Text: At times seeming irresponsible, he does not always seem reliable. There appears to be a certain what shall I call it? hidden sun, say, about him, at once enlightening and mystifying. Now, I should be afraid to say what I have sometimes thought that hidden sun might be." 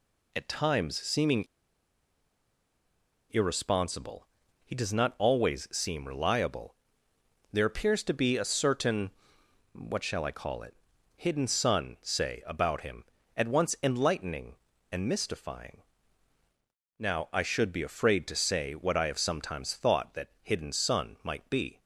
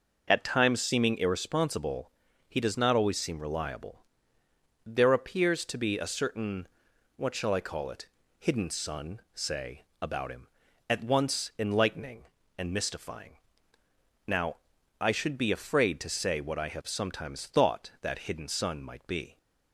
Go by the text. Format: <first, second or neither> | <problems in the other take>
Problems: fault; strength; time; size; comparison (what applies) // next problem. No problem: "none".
second | pauses between "seeming" and "irresponsible"; strong; at 1.4 s; 1.8 s long // pauses between "certain" and "what"; noticeable; at 9.1 s; 0.62 s long; noticeable in the second